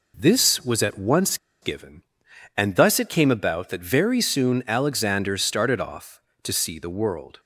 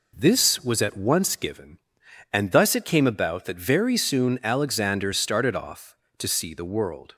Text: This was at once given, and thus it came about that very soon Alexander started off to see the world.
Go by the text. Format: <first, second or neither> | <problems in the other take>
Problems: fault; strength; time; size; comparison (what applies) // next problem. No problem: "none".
second | pauses between "once" and "given"; slight; at 1.3 s; 0.24 s long